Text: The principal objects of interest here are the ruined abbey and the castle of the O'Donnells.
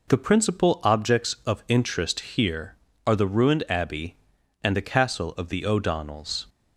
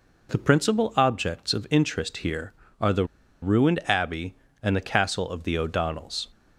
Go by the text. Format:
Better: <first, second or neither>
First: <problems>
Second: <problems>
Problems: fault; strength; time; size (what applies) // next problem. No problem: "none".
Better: first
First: none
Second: pauses between "the" and "ruined"; at 3.0 s; 0.37 s long